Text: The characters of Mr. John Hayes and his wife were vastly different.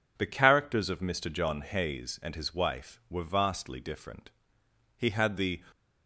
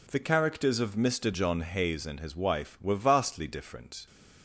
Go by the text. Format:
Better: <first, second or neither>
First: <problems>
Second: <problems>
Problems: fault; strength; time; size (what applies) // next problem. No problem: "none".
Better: second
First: goes on to say "He had the"; noticeable; from 4.9 s on; 0.67 s long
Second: none